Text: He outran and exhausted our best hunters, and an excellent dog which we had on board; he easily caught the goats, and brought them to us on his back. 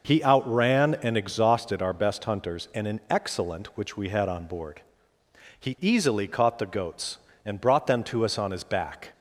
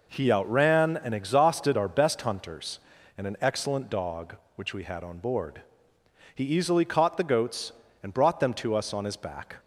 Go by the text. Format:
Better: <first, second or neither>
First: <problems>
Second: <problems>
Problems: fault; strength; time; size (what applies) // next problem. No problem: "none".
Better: second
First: skips "dog"; at 3.7 s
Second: none